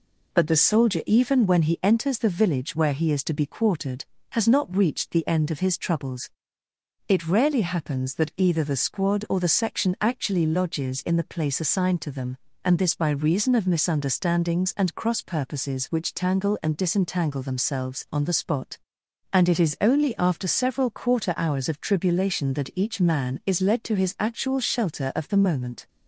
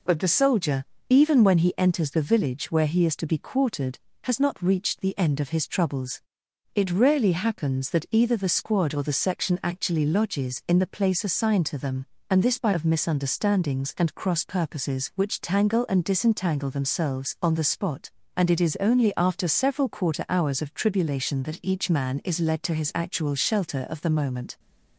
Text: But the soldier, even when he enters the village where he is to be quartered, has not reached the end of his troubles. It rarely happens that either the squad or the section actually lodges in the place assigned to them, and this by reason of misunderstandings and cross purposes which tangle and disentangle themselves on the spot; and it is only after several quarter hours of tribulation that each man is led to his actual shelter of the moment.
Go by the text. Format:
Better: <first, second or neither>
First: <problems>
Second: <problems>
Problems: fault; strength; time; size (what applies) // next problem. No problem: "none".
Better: first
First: none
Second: skips "reason"; at 12.7 s